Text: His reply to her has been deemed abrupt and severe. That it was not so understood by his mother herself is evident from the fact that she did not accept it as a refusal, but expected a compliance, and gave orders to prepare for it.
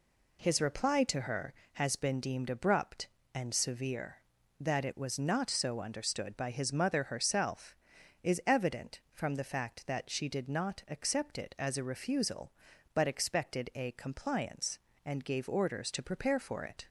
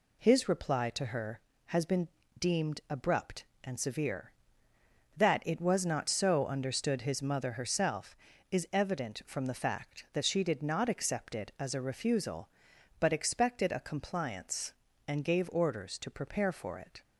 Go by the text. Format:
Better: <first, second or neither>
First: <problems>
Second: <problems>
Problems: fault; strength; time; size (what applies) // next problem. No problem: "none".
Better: first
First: none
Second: pauses between "been" and "deemed"; slight; at 2.0 s; 0.30 s long // skips "by"; at 7.0 s